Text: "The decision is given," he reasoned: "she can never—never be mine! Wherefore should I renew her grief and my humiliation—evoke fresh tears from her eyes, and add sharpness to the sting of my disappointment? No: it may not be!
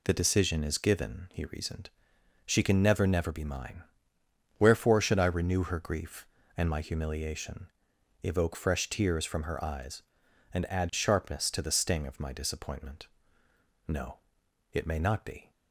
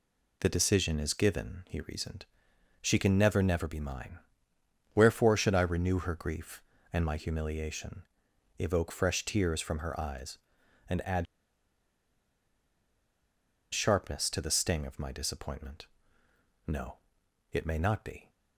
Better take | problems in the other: first | pauses between "add" and "sharpness"; strong; at 11.2 s; 2.4 s long

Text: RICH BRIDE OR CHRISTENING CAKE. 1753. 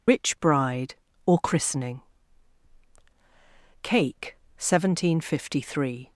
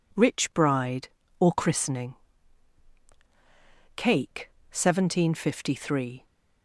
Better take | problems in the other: second | loses the start of "RICH"; at 0.0 s; 110 ms // pauses between "CHRISTENING" and "CAKE"; strong; at 2.0 s; 1.8 s long; strong in the second

